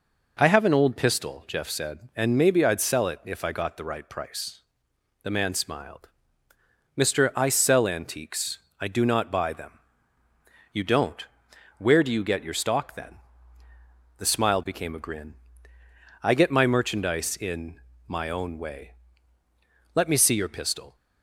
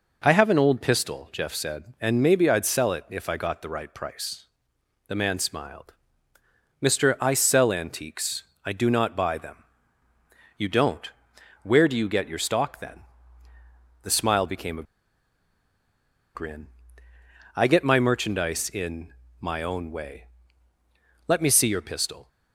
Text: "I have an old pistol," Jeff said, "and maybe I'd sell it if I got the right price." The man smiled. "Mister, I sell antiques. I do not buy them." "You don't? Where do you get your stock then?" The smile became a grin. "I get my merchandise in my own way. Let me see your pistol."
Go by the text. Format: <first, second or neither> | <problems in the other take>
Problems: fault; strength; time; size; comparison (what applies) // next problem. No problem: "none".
first | pauses between "a" and "grin"; strong; at 14.8 s; 1.5 s long // pauses between "in" and "my"; slight; at 19.1 s; 0.26 s long; slight in the first